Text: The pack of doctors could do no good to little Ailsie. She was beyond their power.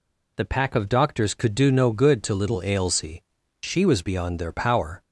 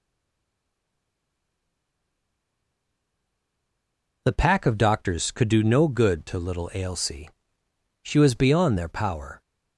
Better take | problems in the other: first | stays silent before the first word; strong; until 4.2 s; 4.2 s long

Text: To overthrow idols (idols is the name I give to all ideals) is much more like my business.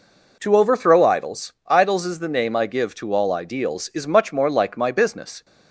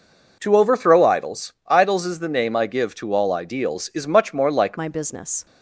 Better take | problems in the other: first | changes voice at "my"; from 4.7 s on; 0.7 s long

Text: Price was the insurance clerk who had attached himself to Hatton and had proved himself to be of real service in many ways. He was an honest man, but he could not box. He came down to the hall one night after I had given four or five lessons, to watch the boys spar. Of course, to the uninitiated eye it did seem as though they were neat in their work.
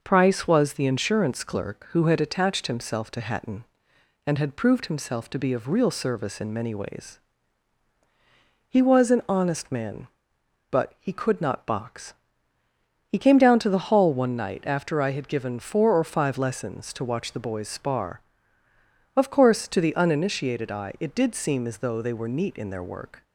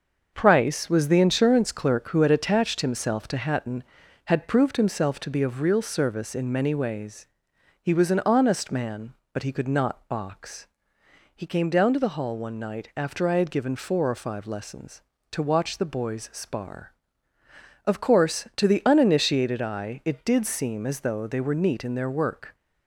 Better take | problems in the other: first | starts louder than the rest; until 1.3 s; 6.5 dB // skips "and"; at 4.0 s

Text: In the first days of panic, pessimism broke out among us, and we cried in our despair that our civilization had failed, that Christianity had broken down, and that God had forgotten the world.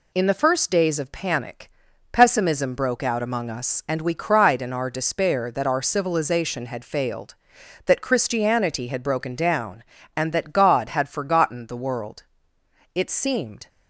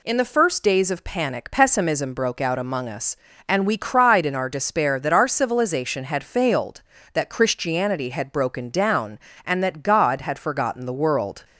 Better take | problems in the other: second | goes on to say "It seemed"; noticeable; from 12.9 s on; 0.74 s long

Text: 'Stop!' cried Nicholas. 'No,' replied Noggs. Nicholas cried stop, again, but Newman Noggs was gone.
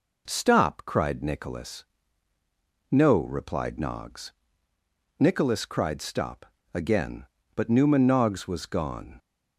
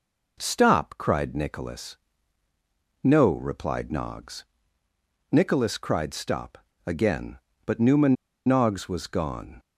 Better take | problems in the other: first | pauses between "Newman" and "Noggs"; slight; at 8.1 s; 0.31 s long

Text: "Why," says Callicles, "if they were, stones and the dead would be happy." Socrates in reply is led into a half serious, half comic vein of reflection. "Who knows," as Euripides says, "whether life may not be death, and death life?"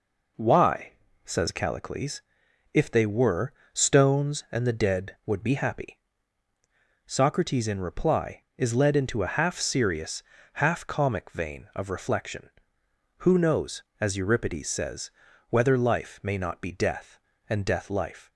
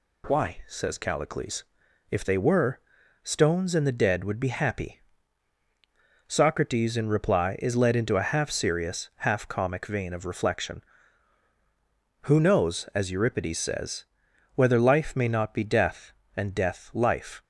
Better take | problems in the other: neither | none

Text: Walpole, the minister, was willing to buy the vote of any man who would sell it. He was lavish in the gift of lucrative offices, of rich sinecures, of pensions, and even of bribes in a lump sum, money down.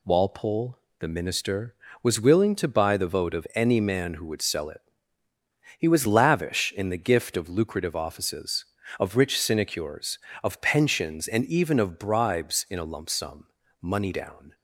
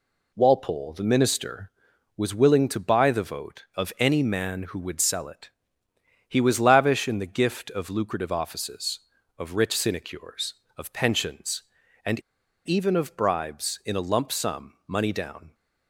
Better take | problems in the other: first | pauses between "and" and "even"; noticeable; at 12.1 s; 0.46 s long

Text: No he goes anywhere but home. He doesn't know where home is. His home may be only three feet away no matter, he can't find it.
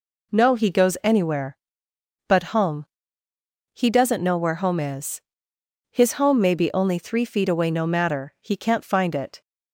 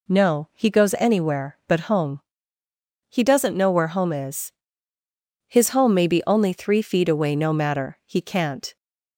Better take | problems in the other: first | stops before "find it"; at 8.7 s

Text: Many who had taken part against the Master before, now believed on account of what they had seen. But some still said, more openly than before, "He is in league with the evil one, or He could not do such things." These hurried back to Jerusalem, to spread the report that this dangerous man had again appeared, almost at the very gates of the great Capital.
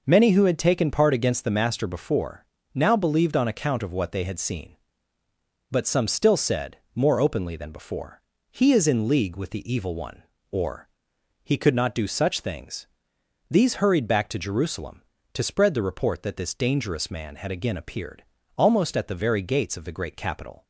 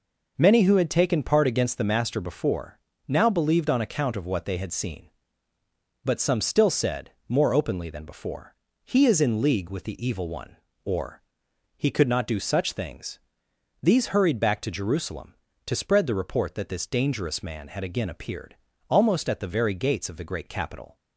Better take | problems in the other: neither | pauses between "or" and "He"; noticeable; the same in both

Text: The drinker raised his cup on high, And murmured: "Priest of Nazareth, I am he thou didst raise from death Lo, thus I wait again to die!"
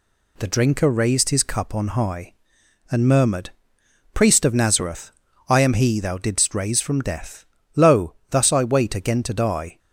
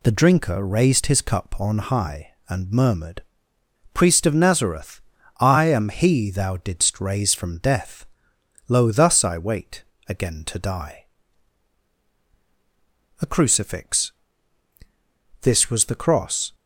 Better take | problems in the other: first | pauses between "death" and "Lo"; noticeable; at 8.0 s; 0.62 s long; slight in the first // pauses between "wait" and "again"; slight; at 9.8 s; 0.24 s long // goes on to say "A CRUCIFIX This was the cross"; strong; from 13.2 s on; 3.3 s long

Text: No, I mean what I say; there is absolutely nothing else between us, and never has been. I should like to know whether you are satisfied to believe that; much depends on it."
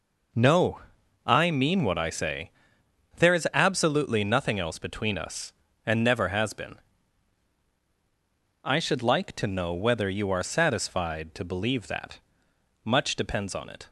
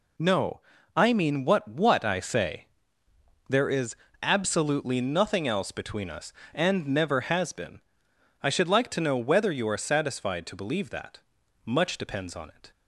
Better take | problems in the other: first | says "what" twice; at 1.6 s // pauses between "is" and "absolutely"; slight; at 3.9 s; 0.28 s long

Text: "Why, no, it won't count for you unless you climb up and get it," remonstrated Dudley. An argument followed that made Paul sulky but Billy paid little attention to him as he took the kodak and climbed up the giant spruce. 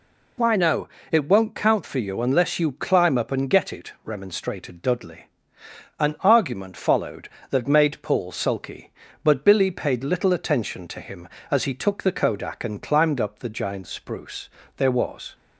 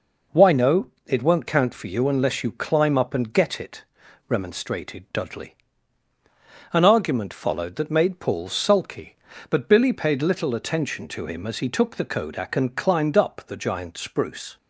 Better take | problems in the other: second | goes on to say "There was"; from 14.7 s on; 0.58 s long

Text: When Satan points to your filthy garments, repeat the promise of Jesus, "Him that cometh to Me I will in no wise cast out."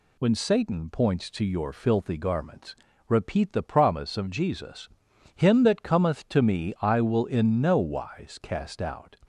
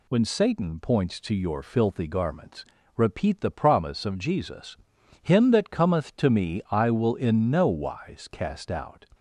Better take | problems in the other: neither | none

